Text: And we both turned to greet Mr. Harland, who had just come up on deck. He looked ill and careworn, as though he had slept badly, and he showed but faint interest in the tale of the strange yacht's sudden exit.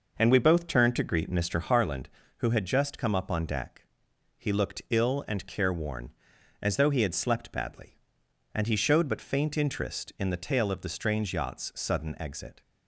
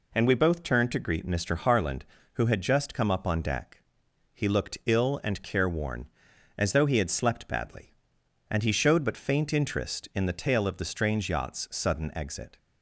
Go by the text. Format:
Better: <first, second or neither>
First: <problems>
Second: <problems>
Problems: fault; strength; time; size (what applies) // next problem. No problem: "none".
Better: second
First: starts louder than the rest; noticeable; until 1.8 s; 5.5 dB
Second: none